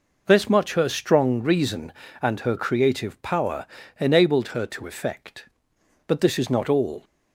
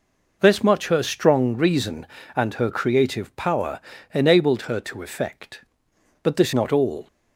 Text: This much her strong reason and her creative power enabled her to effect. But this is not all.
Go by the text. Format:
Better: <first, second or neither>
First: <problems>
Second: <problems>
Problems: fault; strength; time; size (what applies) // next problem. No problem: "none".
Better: first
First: pauses between "power" and "enabled"; slight; at 3.6 s; 0.32 s long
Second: pauses between "power" and "enabled"; slight; at 3.8 s; 0.32 s long // skips "is"; at 6.5 s